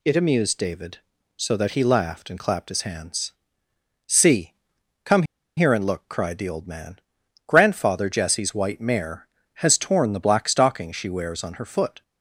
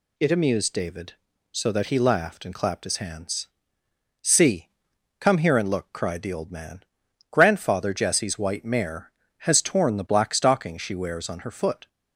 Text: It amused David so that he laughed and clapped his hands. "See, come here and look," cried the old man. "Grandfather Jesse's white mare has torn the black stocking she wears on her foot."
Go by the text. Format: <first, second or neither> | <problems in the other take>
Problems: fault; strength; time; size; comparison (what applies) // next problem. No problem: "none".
second | pauses between "come" and "here"; slight; at 5.2 s; 0.34 s long